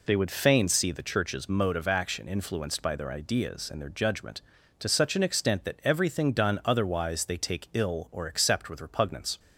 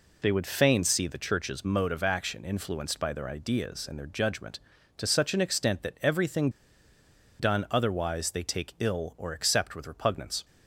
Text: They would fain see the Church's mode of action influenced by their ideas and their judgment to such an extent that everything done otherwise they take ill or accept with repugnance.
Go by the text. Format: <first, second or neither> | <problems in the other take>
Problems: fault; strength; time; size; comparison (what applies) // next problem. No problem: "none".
first | pauses between "everything" and "done"; noticeable; at 6.4 s; 0.90 s long